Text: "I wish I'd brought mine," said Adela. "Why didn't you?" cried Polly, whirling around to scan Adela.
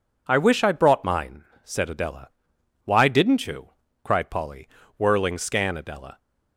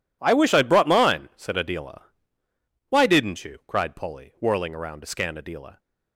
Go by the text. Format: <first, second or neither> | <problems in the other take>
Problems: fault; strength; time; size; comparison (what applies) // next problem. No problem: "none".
second | skips "around to"; at 5.3 s